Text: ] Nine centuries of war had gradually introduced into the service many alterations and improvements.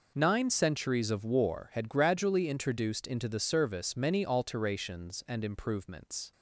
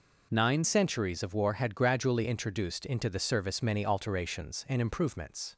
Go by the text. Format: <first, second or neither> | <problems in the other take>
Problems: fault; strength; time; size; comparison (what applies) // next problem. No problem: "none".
first | changes voice at "centuries"; from 0.6 s on; 4.9 s long